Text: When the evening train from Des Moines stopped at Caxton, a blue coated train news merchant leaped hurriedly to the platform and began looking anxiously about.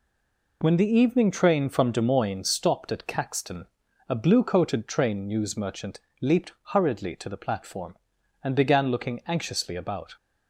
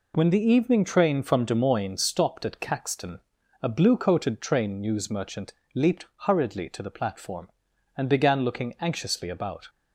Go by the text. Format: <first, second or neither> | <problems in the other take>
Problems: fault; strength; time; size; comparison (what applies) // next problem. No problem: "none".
second | stays silent before the first word; slight; until 0.6 s; 0.6 s long // pauses between "merchant" and "leaped"; slight; at 5.9 s; 0.24 s long; slight in the second